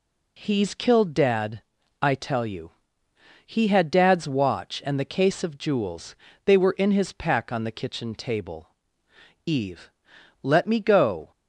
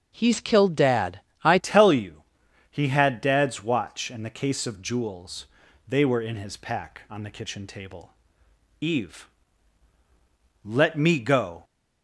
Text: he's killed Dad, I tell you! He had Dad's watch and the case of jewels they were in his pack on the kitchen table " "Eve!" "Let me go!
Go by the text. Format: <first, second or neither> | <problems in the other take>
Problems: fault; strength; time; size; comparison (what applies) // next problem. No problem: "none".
first | starts louder than the rest; strong; until 1.1 s; 7 dB // changes voice at "tell"; from 1.6 s on; 10.0 s long // pauses between "jewels" and "they"; at 5.4 s; 0.42 s long; slight in the first